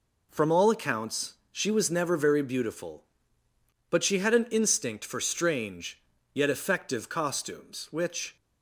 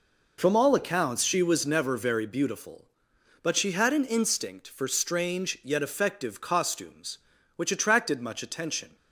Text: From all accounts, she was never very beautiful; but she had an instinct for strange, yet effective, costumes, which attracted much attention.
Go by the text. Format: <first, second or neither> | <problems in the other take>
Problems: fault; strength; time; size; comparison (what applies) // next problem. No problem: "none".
second | stops before "attracted much attention"; at 8.3 s